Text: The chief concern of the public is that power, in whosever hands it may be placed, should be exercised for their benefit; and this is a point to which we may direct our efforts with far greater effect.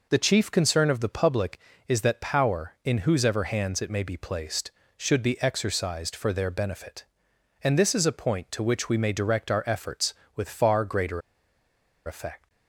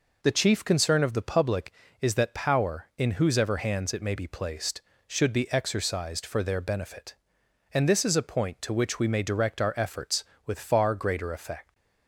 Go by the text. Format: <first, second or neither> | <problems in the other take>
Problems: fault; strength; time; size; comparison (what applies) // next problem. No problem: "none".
second | pauses between "greater" and "effect"; noticeable; at 11.2 s; 0.86 s long